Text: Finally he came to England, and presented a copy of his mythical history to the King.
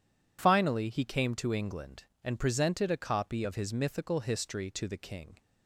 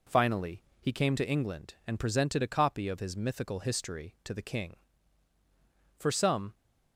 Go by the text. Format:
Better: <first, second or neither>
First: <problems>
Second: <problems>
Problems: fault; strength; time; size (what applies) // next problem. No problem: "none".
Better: first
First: none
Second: pauses between "Finally" and "he"; slight; at 0.6 s; 0.18 s long // goes on to say "For some"; from 5.9 s on; 0.58 s long